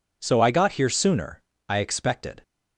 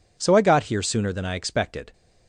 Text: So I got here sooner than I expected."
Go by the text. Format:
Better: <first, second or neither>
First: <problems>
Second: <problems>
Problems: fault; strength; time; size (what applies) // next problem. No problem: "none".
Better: second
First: skips "than"; at 1.5 s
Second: none